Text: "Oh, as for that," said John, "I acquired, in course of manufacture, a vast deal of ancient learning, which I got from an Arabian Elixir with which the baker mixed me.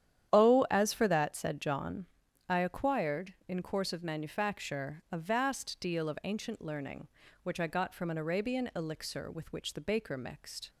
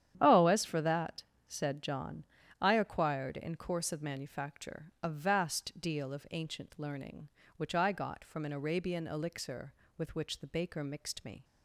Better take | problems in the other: second | starts louder than the rest; strong; until 1.3 s; 10 dB; strong in the second // stops before "me"; at 10.6 s

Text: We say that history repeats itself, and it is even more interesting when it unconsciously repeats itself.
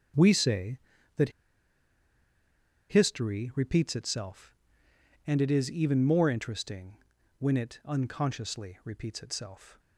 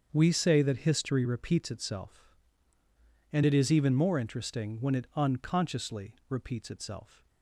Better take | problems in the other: second | starts louder than the rest; until 3.1 s; 7 dB; also in the second // pauses between "that" and "history"; strong; at 1.2 s; 1.6 s long // pauses between "interesting" and "when"; at 6.9 s; 0.42 s long

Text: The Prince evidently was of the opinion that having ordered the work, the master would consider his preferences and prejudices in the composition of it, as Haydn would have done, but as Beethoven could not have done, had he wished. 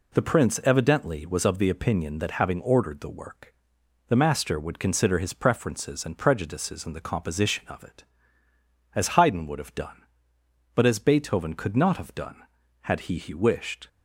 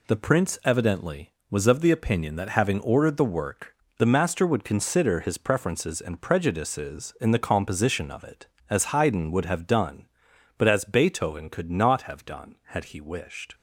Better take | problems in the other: second | says "he" twice; at 13.1 s

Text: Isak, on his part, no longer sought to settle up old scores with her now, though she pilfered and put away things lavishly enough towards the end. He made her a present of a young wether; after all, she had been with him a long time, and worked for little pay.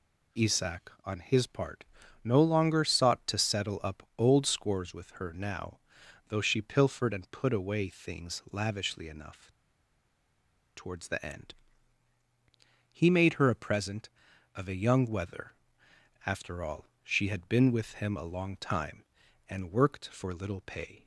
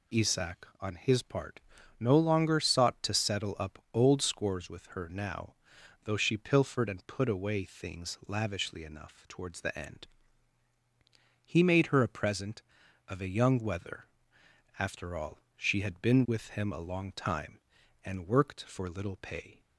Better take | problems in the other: second | pauses between "enough" and "towards"; strong; at 9.4 s; 1.2 s long

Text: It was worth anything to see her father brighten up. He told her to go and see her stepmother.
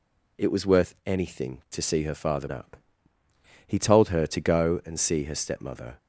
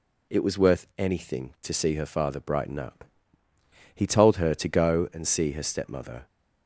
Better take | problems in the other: second | skips "brighten"; at 2.4 s

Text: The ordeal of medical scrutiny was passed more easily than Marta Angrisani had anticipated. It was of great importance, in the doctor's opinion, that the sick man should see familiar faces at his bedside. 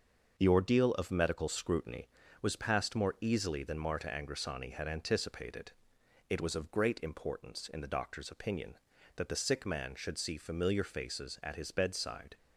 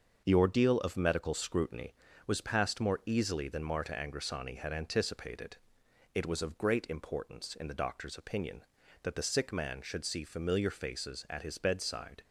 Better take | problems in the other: neither | starts louder than the rest; the same in both

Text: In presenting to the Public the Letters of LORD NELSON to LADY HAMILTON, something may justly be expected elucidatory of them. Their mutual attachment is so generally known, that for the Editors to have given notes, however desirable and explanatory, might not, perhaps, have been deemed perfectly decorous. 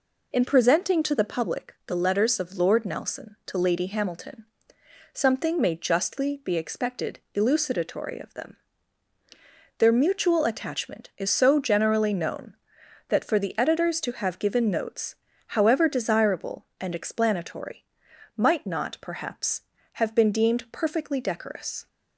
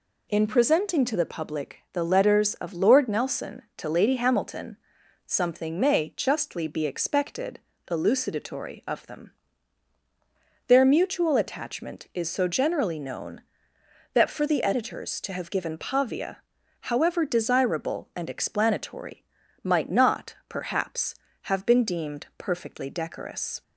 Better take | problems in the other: first | pauses between "expected" and "elucidatory"; slight; at 7.6 s; 0.30 s long; slight in the first // says "pavia" for "notes"; at 15.7 s

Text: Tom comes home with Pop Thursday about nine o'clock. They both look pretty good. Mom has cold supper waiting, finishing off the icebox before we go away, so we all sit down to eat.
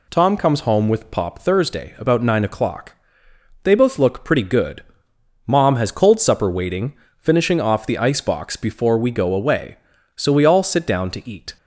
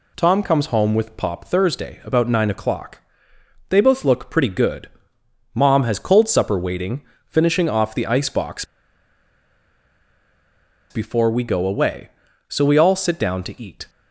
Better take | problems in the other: first | pauses between "icebox" and "before"; strong; at 8.6 s; 2.2 s long

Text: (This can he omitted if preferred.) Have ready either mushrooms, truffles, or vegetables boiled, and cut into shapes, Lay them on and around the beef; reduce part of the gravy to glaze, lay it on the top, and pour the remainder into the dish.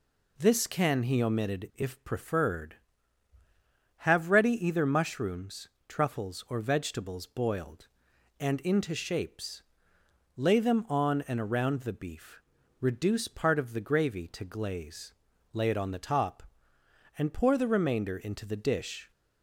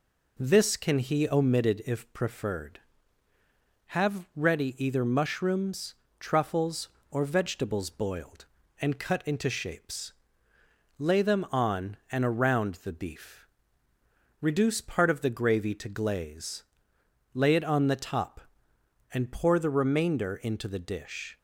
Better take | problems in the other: second | skips "cut"; at 8.6 s

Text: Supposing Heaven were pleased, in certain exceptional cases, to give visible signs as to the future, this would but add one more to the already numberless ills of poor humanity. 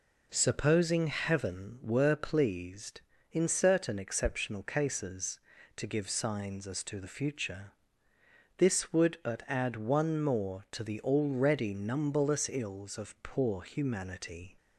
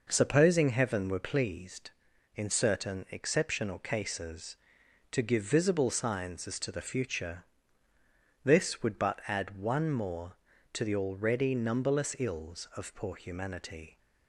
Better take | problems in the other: second | skips "visible"; at 6.0 s

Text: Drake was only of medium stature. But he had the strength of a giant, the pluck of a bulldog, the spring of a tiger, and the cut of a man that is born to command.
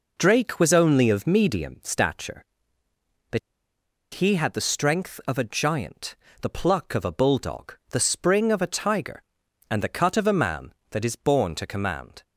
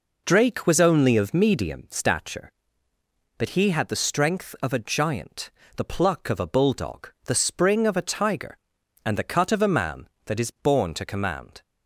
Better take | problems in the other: second | pauses between "But" and "he"; noticeable; at 3.3 s; 0.75 s long

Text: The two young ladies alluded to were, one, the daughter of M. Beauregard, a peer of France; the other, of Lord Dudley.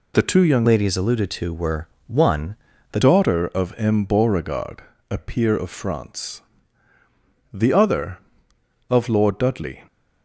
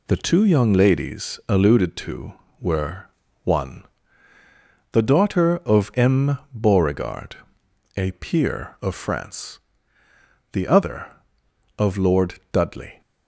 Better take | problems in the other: second | changes voice from "ladies" to "the"; from 0.6 to 2.9 s; 2.3 s long

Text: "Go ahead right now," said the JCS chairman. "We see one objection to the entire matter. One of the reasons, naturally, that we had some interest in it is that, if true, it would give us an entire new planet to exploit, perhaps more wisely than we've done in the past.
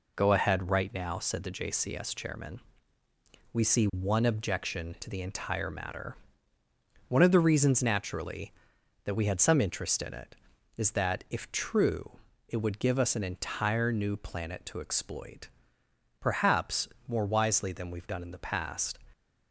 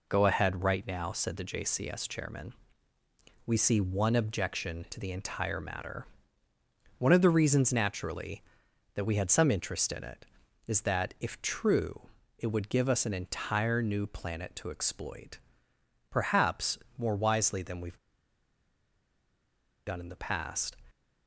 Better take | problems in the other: first | pauses between "perhaps" and "more"; slight; at 16.7 s; 0.18 s long; slight in the first // pauses between "we've" and "done"; strong; at 17.9 s; 1.8 s long

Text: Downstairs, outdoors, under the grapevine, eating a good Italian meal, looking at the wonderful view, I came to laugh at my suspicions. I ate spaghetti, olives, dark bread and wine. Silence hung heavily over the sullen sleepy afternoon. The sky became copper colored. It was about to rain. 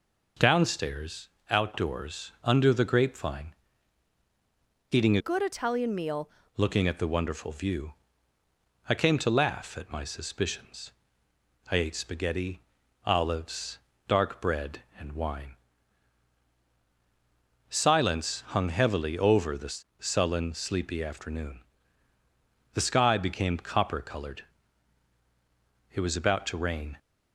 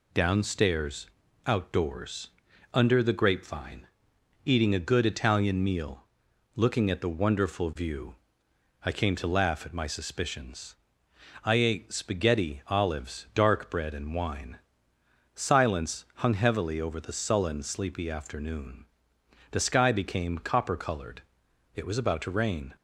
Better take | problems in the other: second | changes voice from "good" to "meal"; from 5.1 to 6.2 s; 1.1 s long // pauses between "the" and "sullen"; slight; at 19.7 s; 0.22 s long

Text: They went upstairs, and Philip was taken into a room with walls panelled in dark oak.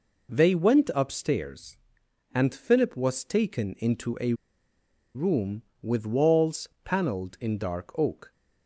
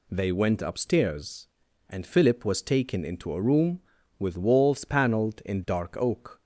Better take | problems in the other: second | pauses between "a" and "room"; noticeable; at 4.3 s; 0.80 s long // pauses between "walls" and "panelled"; slight; at 6.6 s; 0.16 s long

